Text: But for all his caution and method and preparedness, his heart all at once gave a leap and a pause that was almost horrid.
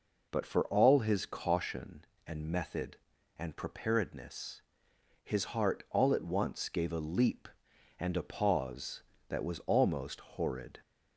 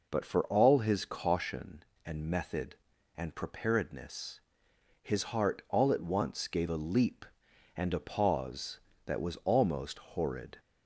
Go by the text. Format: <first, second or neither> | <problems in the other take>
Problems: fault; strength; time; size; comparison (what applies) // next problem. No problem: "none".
neither | none